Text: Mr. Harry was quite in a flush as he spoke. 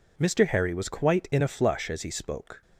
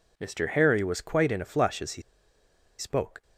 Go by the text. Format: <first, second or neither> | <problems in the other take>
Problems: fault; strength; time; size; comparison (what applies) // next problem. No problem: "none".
first | pauses between "he" and "spoke"; noticeable; at 2.0 s; 0.77 s long